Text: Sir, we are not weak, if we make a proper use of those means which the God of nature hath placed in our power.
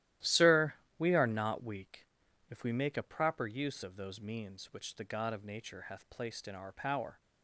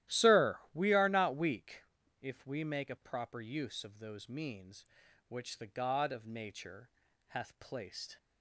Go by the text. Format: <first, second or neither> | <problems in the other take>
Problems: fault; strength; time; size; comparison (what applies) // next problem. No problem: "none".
first | starts louder than the rest; strong; until 1.2 s; 13.5 dB; strong in the first // pauses between "nature" and "hath"; at 6.8 s; 0.40 s long // stops before "in our power"; at 8.1 s